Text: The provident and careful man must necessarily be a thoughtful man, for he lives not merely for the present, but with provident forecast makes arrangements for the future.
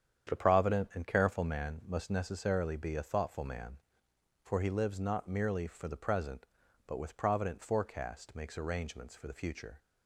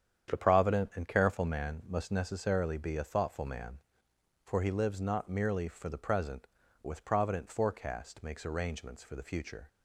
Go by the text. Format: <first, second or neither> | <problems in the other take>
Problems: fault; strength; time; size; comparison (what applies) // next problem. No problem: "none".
first | starts louder than the rest; strong; until 1.3 s; 8.5 dB; strong in the first // skips "but"; at 6.6 s